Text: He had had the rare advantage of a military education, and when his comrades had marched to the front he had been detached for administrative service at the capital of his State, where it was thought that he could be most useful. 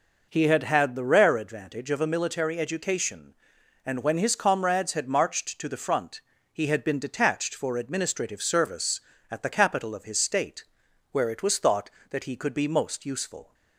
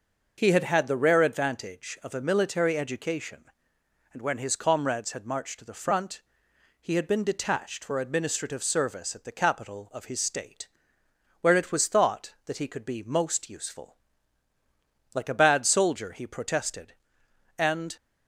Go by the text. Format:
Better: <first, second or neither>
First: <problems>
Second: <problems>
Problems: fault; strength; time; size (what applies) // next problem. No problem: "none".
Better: first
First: pauses between "front" and "he"; slight; at 6.2 s; 0.32 s long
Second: pauses between "front" and "he"; noticeable; at 6.2 s; 0.58 s long // goes on to say "Like a bad soldier he protested and"; strong; from 15.1 s on; 2.8 s long